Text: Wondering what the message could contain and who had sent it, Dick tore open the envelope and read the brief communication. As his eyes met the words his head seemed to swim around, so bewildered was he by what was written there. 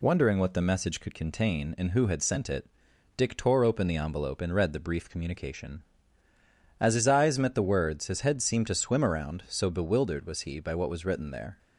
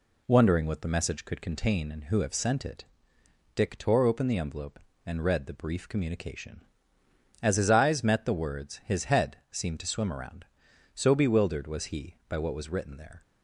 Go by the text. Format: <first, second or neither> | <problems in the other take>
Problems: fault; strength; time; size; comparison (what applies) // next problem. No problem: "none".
first | says "have" for "had"; at 2.1 s // pauses between "head" and "seemed"; slight; at 9.3 s; 0.16 s long